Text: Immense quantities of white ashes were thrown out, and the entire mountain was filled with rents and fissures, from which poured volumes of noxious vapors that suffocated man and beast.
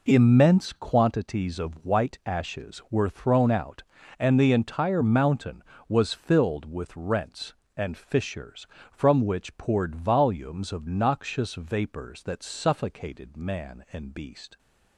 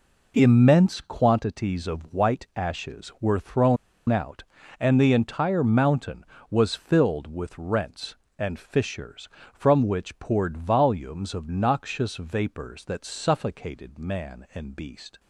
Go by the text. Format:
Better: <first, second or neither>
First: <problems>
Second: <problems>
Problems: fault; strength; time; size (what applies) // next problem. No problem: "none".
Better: first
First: none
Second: pauses between "thrown" and "out"; slight; at 3.7 s; 0.33 s long